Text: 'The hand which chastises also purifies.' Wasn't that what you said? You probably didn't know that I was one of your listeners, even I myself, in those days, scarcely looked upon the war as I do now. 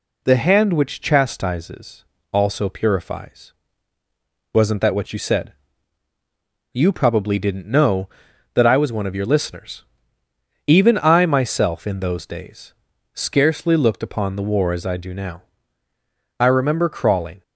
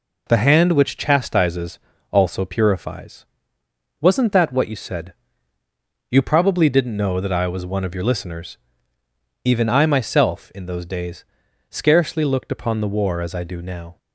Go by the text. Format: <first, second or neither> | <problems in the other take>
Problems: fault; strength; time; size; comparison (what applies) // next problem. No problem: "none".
second | pauses between "chastises" and "also"; slight; at 2.0 s; 0.28 s long; slight in the second // goes on to say "I remember crawling"; noticeable; from 16.3 s on; 1.0 s long